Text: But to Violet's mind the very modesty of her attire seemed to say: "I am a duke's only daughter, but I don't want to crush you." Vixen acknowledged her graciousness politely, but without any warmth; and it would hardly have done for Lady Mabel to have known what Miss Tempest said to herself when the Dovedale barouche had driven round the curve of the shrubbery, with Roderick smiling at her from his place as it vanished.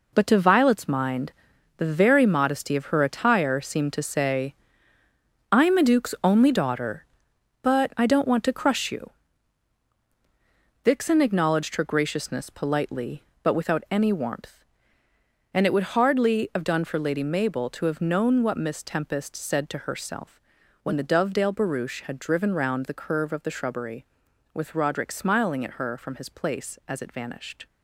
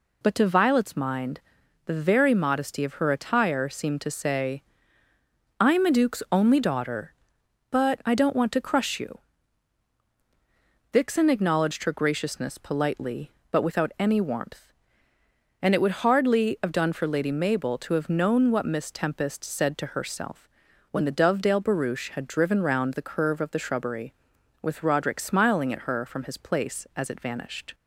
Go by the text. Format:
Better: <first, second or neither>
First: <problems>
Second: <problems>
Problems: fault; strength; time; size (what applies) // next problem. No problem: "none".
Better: second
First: gets quieter; strong; throughout; 10 dB // pauses between "mind" and "the"; noticeable; at 1.3 s; 0.46 s long // pauses between "herself" and "when"; at 20.3 s; 0.44 s long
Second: pauses between "mind" and "the"; noticeable; at 1.4 s; 0.46 s long // pauses between "herself" and "when"; at 20.4 s; 0.44 s long